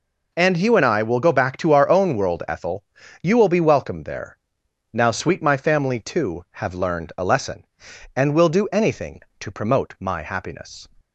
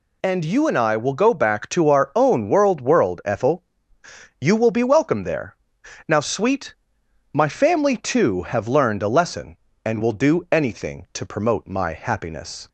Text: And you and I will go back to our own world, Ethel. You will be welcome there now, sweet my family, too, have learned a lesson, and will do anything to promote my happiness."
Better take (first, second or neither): first